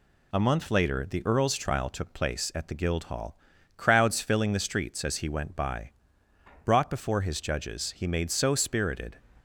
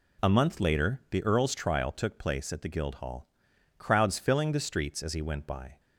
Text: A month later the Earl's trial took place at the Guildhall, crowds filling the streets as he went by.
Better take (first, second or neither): second